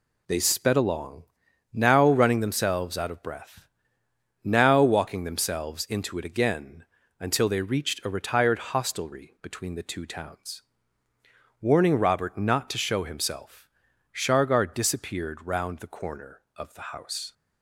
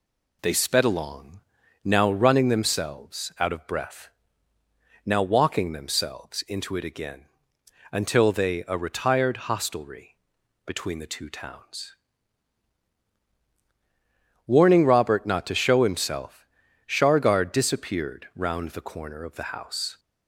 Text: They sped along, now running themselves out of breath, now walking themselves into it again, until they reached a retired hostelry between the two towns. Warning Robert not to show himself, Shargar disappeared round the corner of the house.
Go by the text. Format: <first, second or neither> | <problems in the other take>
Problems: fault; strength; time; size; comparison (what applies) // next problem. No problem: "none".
first | skips "reached"; at 8.6 s // pauses between "hostelry" and "between"; noticeable; at 10.1 s; 0.50 s long